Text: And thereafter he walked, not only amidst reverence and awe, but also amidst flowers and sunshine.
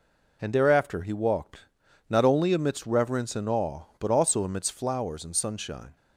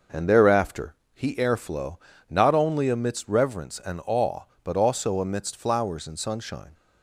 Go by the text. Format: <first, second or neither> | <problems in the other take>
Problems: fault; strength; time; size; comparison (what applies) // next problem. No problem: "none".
first | pauses between "thereafter" and "he"; slight; at 0.9 s; 0.20 s long // says "airflow" for "walked"; at 1.3 s